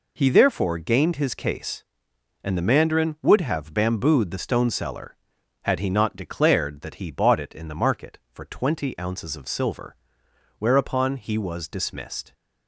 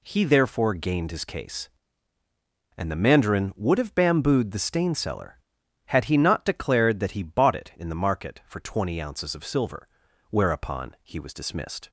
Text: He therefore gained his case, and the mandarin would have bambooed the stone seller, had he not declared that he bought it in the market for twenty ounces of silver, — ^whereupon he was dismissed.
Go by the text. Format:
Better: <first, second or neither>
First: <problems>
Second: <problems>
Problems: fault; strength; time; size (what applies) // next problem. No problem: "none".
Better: first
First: none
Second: says "stain" for "stone"; at 4.5 s